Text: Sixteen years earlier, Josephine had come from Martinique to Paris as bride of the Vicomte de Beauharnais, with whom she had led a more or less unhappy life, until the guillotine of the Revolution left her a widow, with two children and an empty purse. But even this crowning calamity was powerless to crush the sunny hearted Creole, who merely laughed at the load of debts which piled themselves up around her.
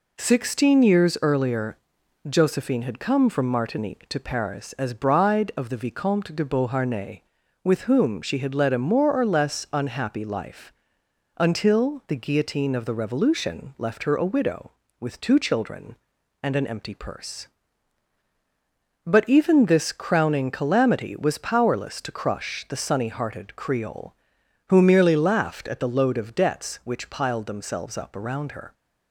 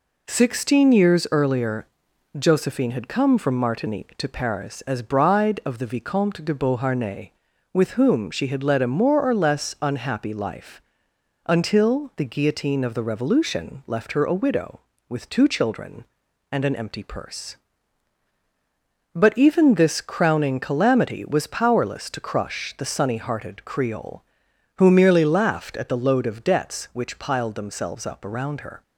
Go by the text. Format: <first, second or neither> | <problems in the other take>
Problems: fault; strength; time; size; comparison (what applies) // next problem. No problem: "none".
neither | none